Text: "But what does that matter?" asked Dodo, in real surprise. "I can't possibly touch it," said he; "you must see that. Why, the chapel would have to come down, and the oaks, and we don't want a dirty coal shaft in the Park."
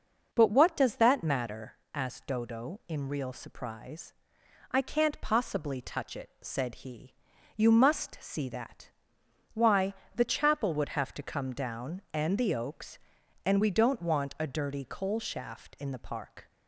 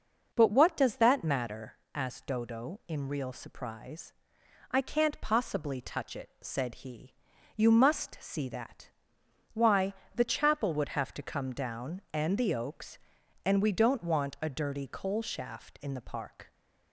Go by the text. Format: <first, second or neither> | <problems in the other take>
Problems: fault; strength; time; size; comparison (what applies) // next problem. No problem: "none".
neither | none